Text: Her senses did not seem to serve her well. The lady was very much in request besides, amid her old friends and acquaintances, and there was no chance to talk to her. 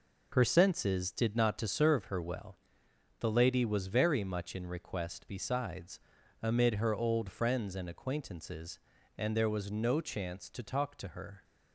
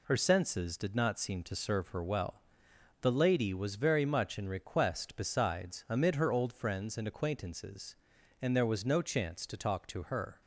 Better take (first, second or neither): second